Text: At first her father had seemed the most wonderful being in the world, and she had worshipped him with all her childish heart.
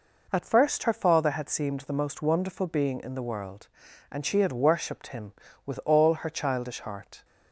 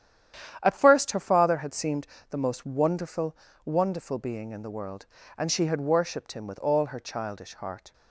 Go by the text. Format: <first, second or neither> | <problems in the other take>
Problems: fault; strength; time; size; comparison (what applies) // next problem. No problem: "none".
first | starts louder than the rest; strong; until 1.6 s; 10 dB // pauses between "seemed" and "the"; slight; at 2.0 s; 0.24 s long // says "wonderful" twice; at 3.6 s